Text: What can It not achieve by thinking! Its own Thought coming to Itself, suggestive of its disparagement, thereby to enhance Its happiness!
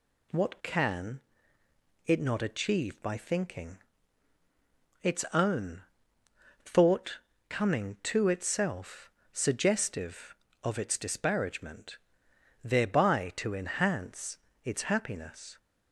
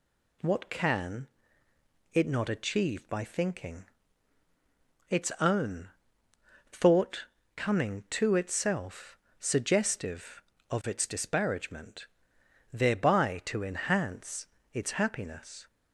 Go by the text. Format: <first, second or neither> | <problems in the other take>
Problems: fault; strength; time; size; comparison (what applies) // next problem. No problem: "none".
neither | pauses between "can" and "It"; noticeable; the same in both // pauses between "own" and "Thought"; noticeable; the same in both // pauses between "Thought" and "coming"; slight; the same in both // pauses between "enhance" and "Its"; slight; the same in both